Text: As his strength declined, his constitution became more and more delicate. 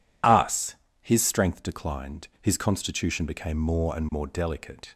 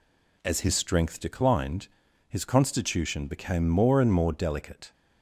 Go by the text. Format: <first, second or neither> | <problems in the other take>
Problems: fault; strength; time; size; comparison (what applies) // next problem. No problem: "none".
second | says "Us" for "As"; at 0.2 s